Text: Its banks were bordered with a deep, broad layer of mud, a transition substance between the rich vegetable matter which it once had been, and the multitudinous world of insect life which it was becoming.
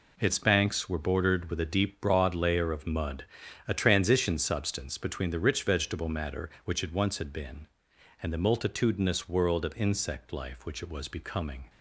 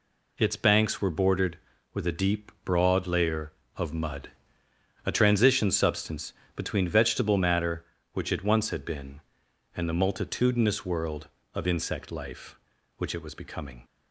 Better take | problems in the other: first | pauses between "substance" and "between"; slight; at 6.3 s; 0.22 s long // skips "the rich"; at 6.8 s

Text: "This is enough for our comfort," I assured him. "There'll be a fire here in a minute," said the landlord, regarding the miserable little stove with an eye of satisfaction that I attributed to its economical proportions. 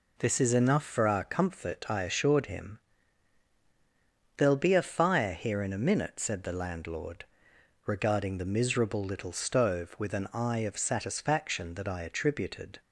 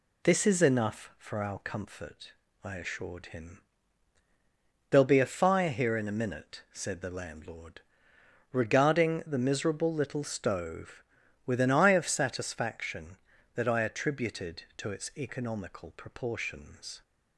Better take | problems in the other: second | stops before "to its economical proportions"; at 12.8 s

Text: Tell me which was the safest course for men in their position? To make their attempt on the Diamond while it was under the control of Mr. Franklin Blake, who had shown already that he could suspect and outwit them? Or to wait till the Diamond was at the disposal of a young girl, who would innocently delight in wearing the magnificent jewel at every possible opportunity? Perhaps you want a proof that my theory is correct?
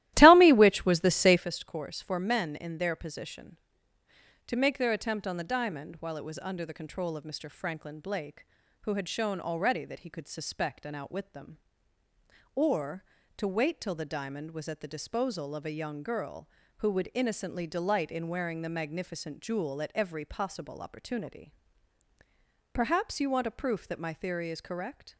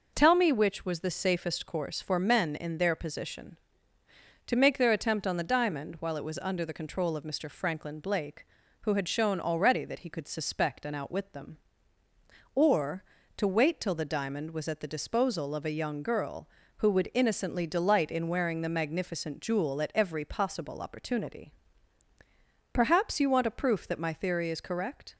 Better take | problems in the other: second | starts louder than the rest; strong; until 1.5 s; 15 dB

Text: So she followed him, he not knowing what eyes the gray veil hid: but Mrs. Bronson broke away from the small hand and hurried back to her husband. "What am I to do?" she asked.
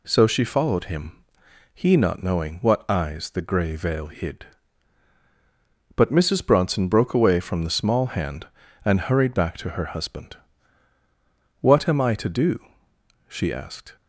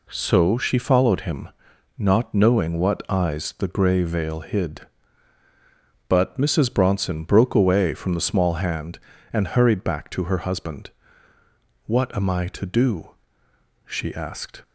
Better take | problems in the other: first | skips "he"; at 1.7 s

